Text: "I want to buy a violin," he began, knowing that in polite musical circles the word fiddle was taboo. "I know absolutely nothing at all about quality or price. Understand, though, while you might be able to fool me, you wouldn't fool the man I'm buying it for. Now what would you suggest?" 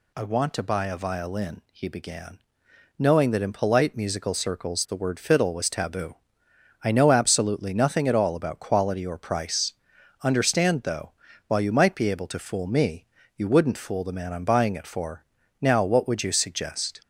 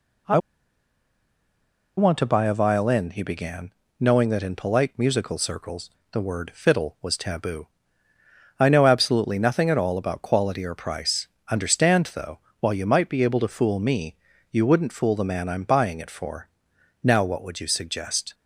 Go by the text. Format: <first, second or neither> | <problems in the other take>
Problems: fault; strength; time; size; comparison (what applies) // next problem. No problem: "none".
first | pauses between "I" and "want"; strong; at 0.3 s; 1.5 s long // pauses between "circles" and "the"; slight; at 5.8 s; 0.22 s long